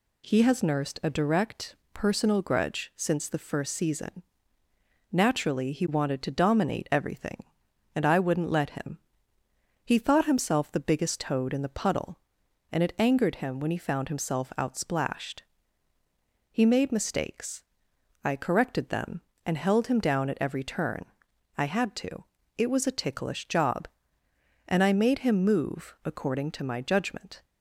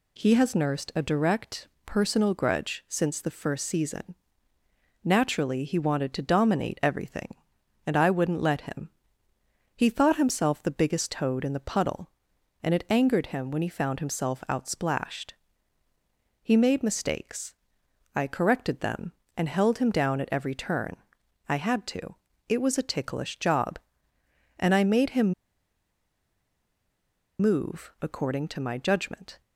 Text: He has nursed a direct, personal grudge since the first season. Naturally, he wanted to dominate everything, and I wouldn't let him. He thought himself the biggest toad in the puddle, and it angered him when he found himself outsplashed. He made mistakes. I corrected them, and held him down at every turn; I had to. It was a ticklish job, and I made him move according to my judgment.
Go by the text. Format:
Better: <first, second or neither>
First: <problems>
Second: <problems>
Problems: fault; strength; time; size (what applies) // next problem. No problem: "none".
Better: first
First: none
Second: pauses between "him" and "move"; strong; at 25.3 s; 2.0 s long